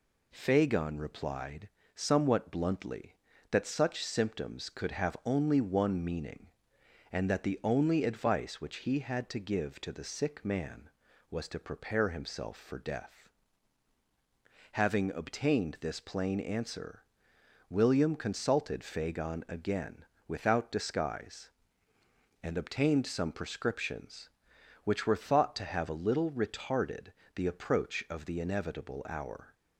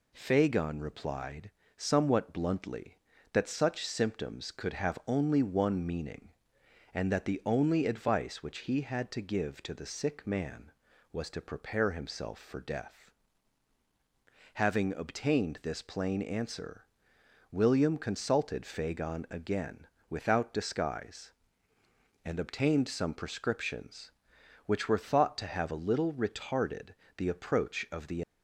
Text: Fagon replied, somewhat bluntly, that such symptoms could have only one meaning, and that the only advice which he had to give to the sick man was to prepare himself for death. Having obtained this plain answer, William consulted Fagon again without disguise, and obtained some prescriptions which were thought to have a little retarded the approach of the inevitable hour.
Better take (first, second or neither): first